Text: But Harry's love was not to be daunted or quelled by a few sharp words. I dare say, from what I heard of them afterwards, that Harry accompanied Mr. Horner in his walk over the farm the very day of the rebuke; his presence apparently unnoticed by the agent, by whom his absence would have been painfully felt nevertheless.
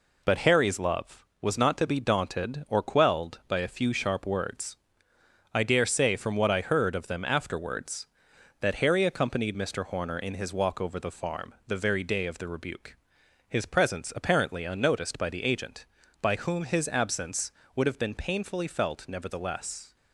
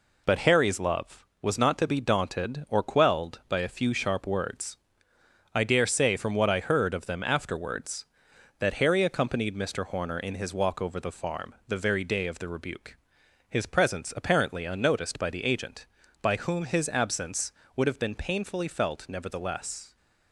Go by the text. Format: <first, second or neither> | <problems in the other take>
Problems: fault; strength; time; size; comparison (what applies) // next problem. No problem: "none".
neither | none